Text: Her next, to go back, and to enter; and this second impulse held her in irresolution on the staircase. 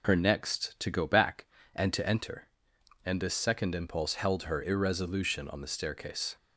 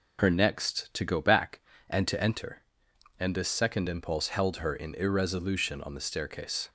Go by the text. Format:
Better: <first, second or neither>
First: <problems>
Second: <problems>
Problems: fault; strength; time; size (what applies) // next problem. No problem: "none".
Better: second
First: skips "in"; at 4.6 s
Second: none